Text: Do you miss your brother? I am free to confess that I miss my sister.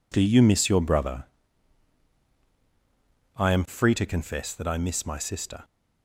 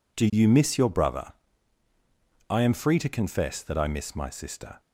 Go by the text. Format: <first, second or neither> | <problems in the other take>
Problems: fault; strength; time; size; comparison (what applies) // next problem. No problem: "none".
neither | none